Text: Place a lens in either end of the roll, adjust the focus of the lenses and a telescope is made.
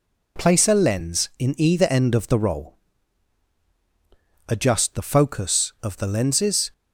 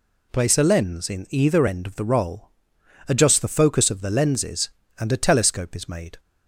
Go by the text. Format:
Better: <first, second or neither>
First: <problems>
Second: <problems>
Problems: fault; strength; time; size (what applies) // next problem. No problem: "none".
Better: second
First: stops before "and a telescope is made"; at 6.7 s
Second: none